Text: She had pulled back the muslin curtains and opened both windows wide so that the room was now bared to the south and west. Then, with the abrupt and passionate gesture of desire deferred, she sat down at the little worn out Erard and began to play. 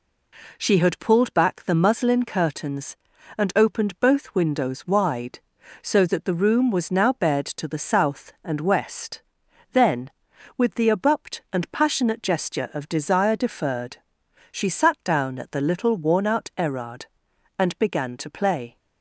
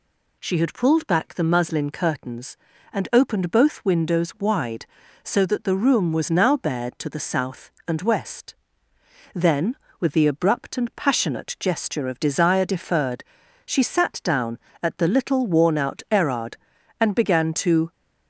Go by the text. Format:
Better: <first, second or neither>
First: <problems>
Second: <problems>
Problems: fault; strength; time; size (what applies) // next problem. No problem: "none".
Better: first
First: none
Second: stops before "play"; at 17.9 s